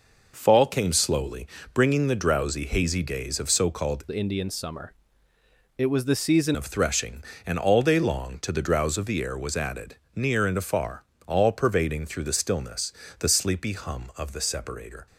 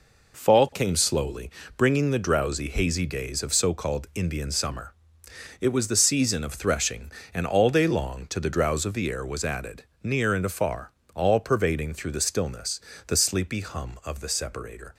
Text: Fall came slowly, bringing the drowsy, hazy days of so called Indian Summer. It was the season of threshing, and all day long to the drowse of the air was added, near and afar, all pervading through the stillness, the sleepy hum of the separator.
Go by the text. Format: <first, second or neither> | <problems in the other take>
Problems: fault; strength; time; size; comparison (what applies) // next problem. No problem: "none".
second | changes voice from "Indian" to "season"; from 4.0 to 6.5 s; 2.5 s long